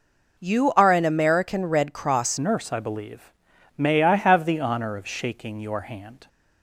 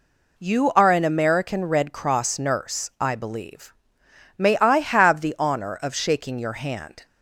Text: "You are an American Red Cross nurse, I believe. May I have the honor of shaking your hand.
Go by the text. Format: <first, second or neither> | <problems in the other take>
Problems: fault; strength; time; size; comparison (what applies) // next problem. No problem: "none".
second | changes voice at "nurse"; from 2.3 s on; 3.9 s long